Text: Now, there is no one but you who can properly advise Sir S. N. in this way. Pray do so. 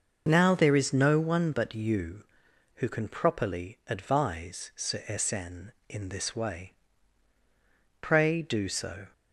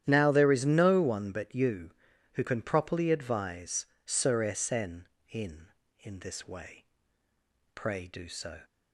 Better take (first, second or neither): first